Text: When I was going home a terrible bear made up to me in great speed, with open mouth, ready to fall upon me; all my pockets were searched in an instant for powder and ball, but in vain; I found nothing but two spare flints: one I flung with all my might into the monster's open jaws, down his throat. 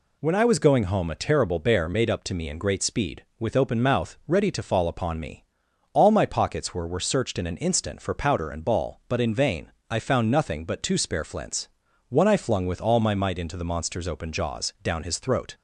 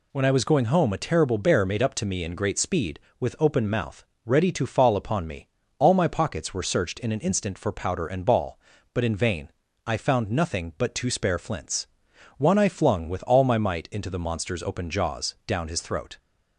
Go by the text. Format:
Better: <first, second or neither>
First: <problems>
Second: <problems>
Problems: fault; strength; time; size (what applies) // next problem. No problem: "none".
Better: second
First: says "were" twice; at 6.8 s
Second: none